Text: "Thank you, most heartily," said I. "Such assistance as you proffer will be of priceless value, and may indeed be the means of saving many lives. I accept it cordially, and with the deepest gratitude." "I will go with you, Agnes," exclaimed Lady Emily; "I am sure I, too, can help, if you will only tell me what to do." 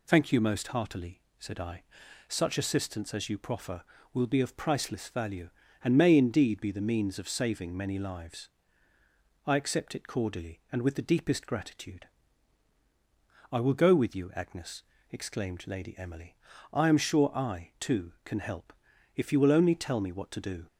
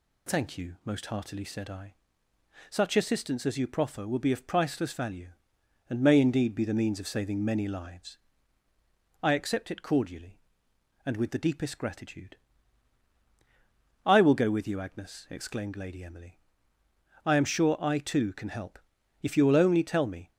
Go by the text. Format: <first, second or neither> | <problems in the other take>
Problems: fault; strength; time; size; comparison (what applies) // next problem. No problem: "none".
first | stops before "what to do"; at 20.3 s